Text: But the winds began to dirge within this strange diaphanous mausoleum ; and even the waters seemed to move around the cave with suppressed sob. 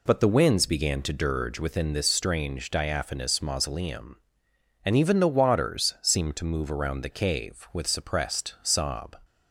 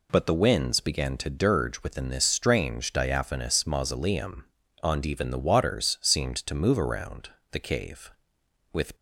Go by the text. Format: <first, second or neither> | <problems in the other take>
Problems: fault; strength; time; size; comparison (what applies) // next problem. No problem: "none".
first | pauses between "around" and "the"; slight; at 7.2 s; 0.24 s long // stops before "suppressed sob"; at 8.9 s